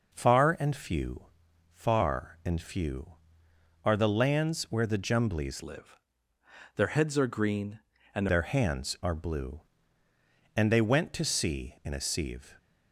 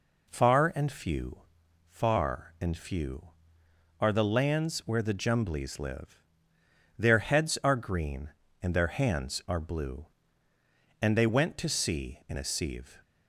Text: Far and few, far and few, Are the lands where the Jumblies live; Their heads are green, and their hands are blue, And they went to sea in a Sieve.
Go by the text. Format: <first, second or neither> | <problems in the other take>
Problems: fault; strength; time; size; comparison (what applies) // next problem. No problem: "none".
second | changes voice from "live" to "and"; from 5.6 to 8.2 s; 2.6 s long